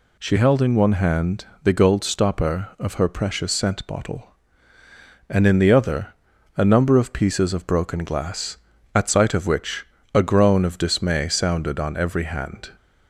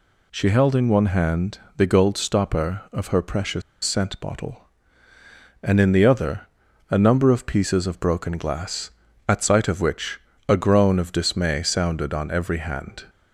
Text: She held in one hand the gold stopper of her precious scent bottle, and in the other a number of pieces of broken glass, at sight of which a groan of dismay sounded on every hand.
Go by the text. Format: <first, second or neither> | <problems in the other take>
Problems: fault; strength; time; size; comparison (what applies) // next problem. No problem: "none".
first | pauses between "hand" and "the"; slight; at 1.5 s; 0.18 s long; slight in the first // pauses between "precious" and "scent"; slight; at 3.6 s; 0.22 s long // pauses between "other" and "a"; at 6.4 s; 0.44 s long; also in the first // pauses between "which" and "a"; slight; at 10.1 s; 0.30 s long; slight in the first